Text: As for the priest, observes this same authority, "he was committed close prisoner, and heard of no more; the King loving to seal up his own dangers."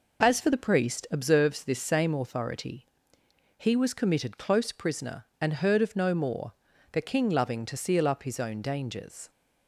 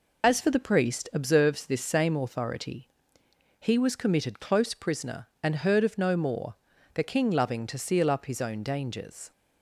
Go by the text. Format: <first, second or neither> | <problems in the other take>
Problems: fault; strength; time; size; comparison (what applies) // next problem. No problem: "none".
first | loses the start of "As"; at 0.2 s; 35 ms